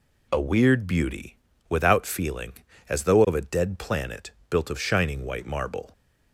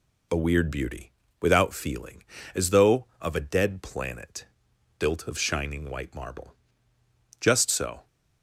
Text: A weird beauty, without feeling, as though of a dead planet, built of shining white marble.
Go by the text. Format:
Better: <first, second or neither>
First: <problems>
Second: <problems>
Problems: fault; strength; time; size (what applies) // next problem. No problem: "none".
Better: first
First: none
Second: goes on to say "Just so"; noticeable; from 7.3 s on; 0.68 s long